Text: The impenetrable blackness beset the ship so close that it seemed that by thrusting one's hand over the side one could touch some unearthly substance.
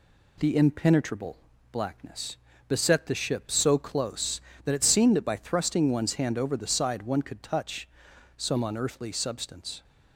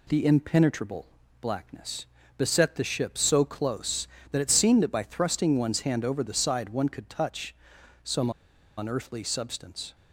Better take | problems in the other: first | pauses between "impenetrable" and "blackness"; slight; at 1.0 s; 0.34 s long; slight in the first // pauses between "blackness" and "beset"; slight; at 2.0 s; 0.32 s long; slight in the first // pauses between "touch" and "some"; noticeable; at 7.5 s; 0.50 s long; noticeable in the first // pauses between "some" and "unearthly"; noticeable; at 8.2 s; 0.47 s long

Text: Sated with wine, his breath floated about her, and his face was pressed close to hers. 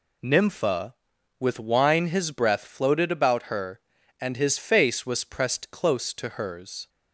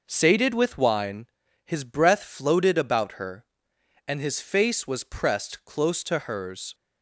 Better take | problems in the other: second | says "Nympha" for "Sated"; at 0.2 s

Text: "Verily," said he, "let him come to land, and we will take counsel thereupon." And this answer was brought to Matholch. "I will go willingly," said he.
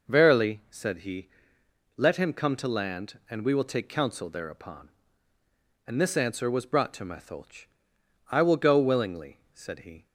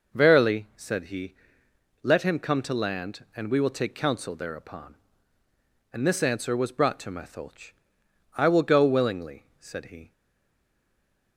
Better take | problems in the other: first | stays silent after the last word; noticeable; from 10.1 s on; 1.2 s long

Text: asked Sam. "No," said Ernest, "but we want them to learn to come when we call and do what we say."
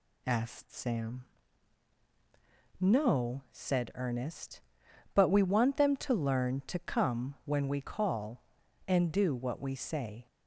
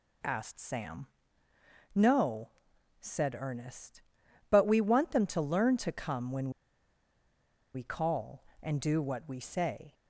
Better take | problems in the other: first | pauses between "when" and "we"; strong; at 6.4 s; 1.2 s long

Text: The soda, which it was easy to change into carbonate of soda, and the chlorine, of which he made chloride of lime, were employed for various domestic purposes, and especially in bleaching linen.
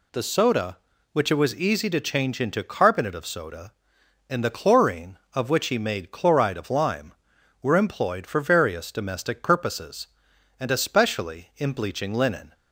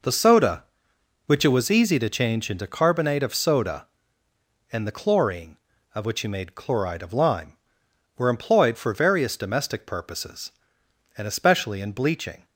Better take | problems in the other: first | stops before "linen"; at 12.4 s

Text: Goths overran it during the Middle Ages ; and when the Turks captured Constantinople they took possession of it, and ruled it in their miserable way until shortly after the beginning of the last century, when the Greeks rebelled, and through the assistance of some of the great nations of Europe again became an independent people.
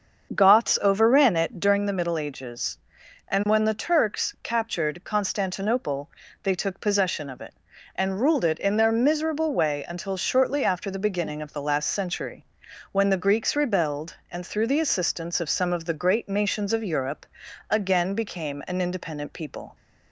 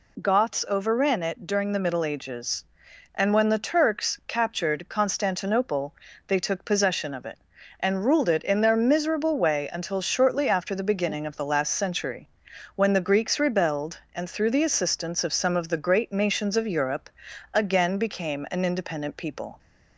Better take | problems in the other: second | starts louder than the rest; until 1.9 s; 7 dB // pauses between "Constantinople" and "they"; slight; at 6.0 s; 0.34 s long; slight in the second // pauses between "Europe" and "again"; at 17.2 s; 0.42 s long; also in the second

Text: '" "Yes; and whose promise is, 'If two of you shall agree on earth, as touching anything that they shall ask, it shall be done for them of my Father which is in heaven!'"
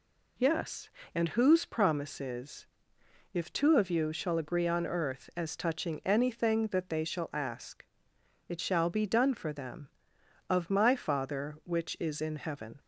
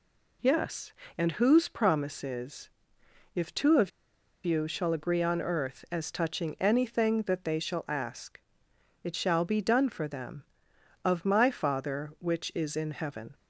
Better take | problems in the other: first | pauses between "of" and "you"; noticeable; at 3.9 s; 0.55 s long

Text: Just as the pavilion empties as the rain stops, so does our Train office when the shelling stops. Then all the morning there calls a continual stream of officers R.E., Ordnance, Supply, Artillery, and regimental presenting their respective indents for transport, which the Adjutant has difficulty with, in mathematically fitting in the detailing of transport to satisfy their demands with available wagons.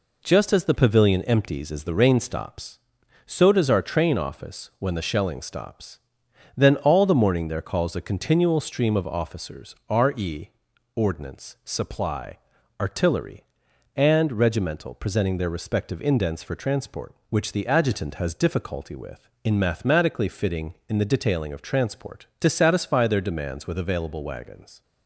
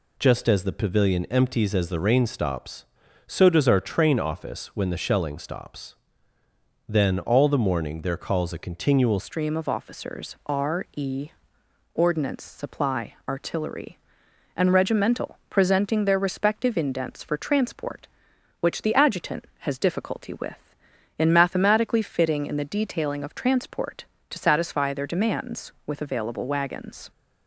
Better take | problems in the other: first | changes voice at "stream"; from 9.1 s on; 17.9 s long

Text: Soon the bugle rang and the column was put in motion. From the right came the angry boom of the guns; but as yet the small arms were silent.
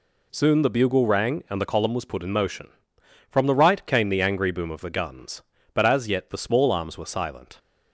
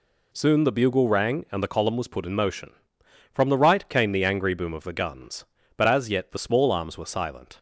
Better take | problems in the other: neither | none

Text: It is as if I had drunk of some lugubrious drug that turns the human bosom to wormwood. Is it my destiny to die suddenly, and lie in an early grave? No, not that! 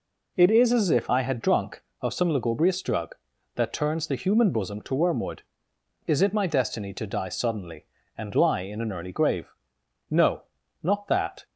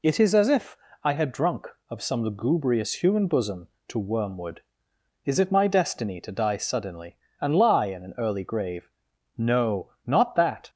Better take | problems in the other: first | pauses between "if" and "I"; slight; at 0.7 s; 0.24 s long // skips "drug that turns the"; at 3.0 s

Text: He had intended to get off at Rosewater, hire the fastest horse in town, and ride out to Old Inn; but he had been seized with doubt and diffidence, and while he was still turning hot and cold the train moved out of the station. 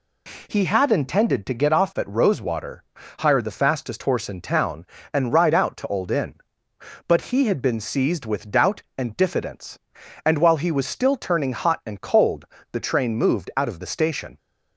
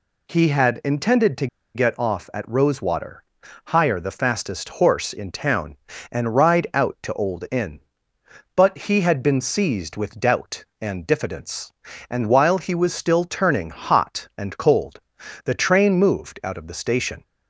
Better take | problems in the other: first | pauses between "to" and "get"; slight; at 1.4 s; 0.27 s long // pauses between "cold" and "the"; at 15.0 s; 0.44 s long; slight in the first

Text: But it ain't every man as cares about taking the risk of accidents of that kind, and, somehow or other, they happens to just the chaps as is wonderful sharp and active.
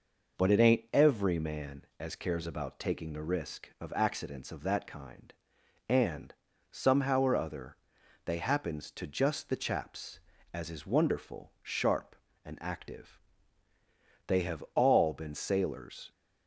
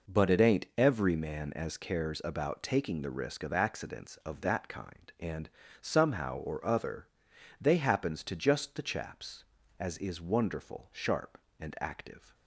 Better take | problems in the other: second | goes on to say "They have all been sailors"; strong; from 14.2 s on; 1.8 s long

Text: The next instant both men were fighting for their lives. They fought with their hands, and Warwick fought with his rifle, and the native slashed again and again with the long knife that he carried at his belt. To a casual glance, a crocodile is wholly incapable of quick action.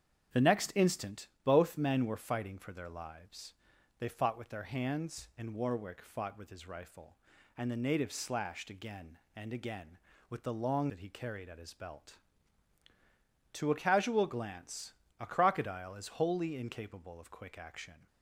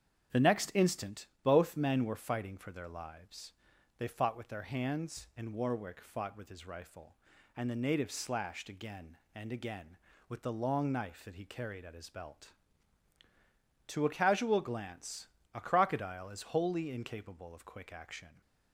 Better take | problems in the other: second | starts louder than the rest; strong; until 1.5 s; 8.5 dB; strong in the second // pauses between "instant" and "both"; slight; at 1.2 s; 0.16 s long; slight in the second // skips "knife"; at 10.8 s

